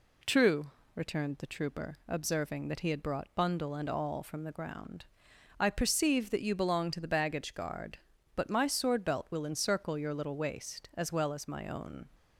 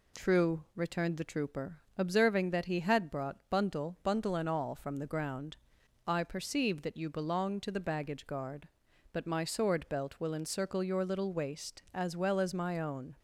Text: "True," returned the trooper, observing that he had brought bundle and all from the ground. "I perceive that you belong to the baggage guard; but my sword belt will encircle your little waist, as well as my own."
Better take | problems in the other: first | says "bundle" twice; at 4.0 s

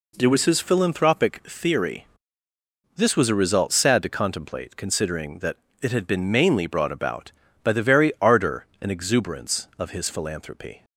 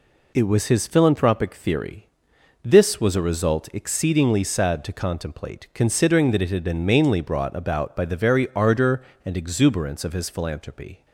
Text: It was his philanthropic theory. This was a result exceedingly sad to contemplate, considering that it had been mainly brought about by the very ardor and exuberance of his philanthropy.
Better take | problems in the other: second | skips "exceedingly"; at 3.7 s // pauses between "that" and "it"; slight; at 5.5 s; 0.26 s long

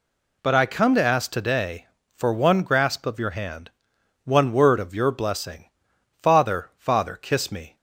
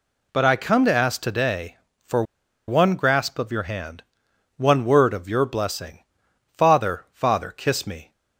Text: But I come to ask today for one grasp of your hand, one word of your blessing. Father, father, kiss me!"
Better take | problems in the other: first | pauses between "for" and "one"; at 2.2 s; 0.44 s long

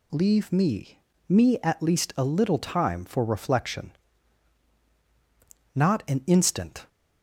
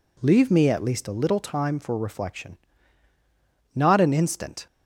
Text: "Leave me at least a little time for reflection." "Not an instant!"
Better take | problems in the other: second | says "me" twice; at 1.2 s

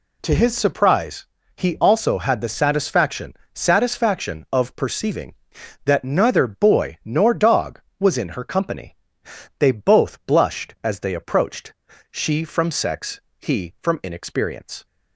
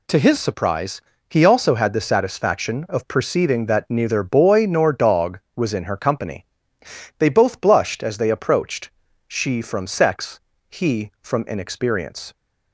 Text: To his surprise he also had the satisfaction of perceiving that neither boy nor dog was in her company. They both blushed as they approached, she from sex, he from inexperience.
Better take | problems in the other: second | pauses between "surprise" and "he"; slight; at 1.2 s; 0.30 s long; slight in the second // says "satisfaction" twice; at 3.5 s

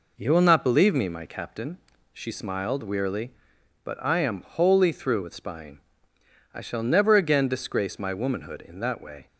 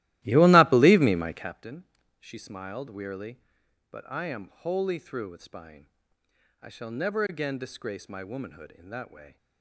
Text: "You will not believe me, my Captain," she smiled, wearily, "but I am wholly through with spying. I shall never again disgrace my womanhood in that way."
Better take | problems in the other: first | starts louder than the rest; strong; until 1.6 s; 16 dB

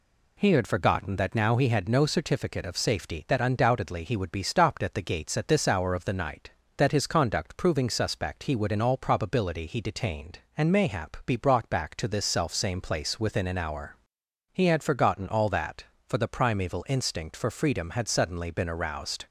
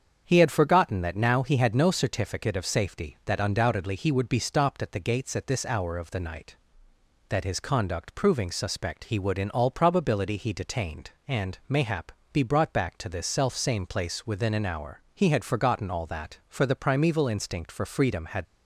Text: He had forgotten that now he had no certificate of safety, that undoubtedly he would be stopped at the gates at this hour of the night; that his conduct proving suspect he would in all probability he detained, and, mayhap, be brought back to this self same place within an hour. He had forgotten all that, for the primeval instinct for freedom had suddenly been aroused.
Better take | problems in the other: first | starts louder than the rest; strong; until 1.2 s; 7.5 dB // stops before "suddenly been aroused"; at 18.4 s

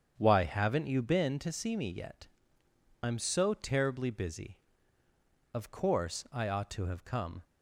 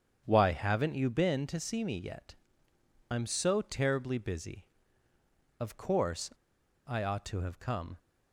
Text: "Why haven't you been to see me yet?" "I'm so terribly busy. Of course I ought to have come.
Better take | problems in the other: first | starts louder than the rest; strong; until 1.2 s; 8 dB; strong in the first // pauses between "course" and "I"; noticeable; at 6.3 s; 0.54 s long

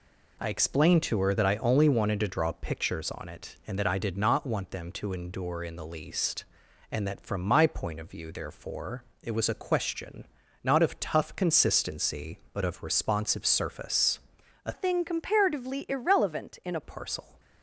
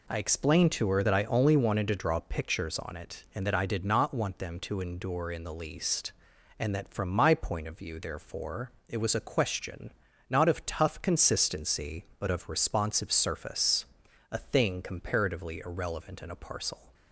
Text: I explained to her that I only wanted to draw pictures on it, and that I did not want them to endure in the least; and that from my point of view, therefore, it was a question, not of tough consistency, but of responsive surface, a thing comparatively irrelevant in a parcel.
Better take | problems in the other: second | changes voice from "thing" to "a"; from 14.7 to 16.8 s; 2.1 s long

